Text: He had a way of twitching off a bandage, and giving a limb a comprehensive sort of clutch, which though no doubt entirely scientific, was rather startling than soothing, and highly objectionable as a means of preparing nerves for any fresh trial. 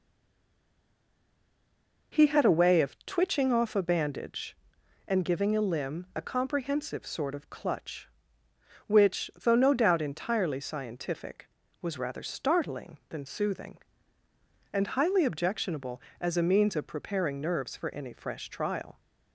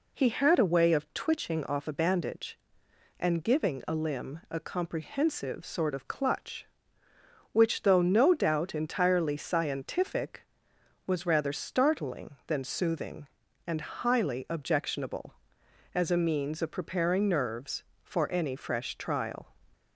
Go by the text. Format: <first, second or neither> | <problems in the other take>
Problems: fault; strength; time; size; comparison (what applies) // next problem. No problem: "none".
second | stays silent before the first word; until 2.1 s; 2.1 s long